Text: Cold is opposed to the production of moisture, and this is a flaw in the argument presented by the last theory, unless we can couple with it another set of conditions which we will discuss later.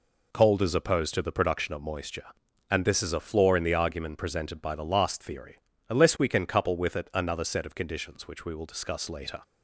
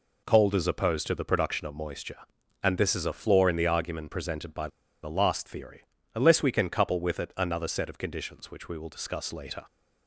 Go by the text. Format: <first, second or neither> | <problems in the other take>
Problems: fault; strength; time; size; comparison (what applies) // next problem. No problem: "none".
first | pauses between "by" and "the"; slight; at 4.6 s; 0.33 s long